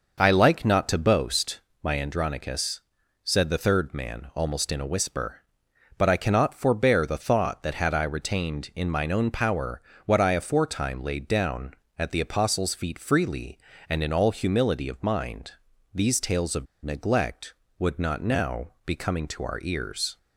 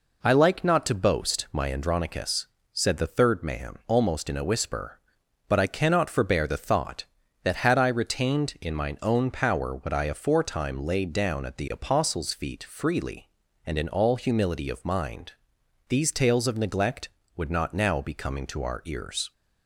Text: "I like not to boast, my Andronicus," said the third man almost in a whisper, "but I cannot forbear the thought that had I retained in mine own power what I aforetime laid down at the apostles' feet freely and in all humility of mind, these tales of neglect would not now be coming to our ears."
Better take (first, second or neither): second